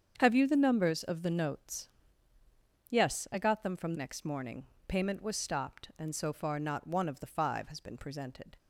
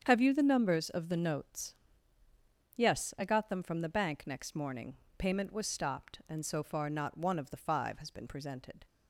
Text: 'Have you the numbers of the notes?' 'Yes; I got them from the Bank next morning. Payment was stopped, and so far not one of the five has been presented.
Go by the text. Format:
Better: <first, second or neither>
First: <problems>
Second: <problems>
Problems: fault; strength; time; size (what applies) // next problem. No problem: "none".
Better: second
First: starts louder than the rest; strong; until 1.1 s; 7.5 dB // skips "the Bank"; at 3.9 s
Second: starts louder than the rest; strong; until 1.0 s; 7.5 dB